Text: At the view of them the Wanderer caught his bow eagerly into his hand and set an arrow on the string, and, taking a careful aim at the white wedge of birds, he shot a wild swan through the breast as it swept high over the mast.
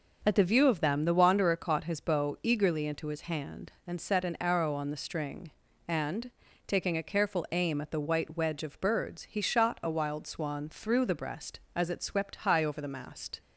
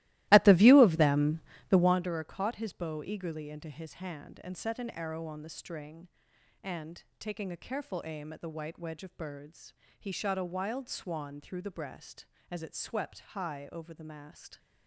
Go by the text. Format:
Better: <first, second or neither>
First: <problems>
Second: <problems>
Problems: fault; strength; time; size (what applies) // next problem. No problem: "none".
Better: first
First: none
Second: starts louder than the rest; strong; until 2.0 s; 17 dB // pauses between "them" and "the"; slight; at 1.4 s; 0.30 s long